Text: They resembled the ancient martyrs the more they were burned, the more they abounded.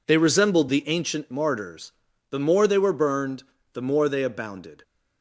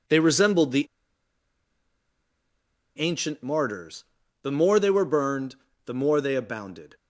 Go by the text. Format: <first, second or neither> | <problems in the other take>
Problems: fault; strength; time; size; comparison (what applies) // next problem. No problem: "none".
first | pauses between "the" and "ancient"; strong; at 0.8 s; 2.1 s long // pauses between "martyrs" and "the"; at 4.0 s; 0.38 s long; also in the first